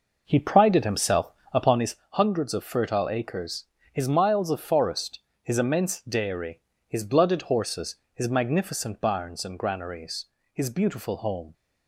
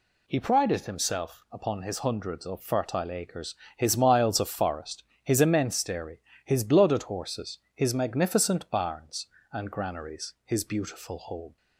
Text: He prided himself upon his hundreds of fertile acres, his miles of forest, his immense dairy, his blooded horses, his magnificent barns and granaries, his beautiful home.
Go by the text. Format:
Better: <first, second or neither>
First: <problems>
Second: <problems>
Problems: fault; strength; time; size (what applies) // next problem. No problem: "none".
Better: second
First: starts louder than the rest; noticeable; until 2.0 s; 5.5 dB // pauses between "himself" and "upon"; slight; at 1.3 s; 0.22 s long // pauses between "his" and "hundreds"; slight; at 1.9 s; 0.16 s long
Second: none